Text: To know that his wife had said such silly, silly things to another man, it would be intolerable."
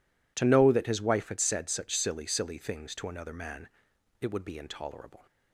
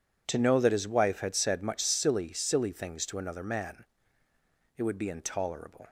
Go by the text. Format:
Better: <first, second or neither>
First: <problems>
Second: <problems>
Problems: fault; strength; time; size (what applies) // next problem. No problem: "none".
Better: first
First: none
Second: says "much" for "such"; at 1.6 s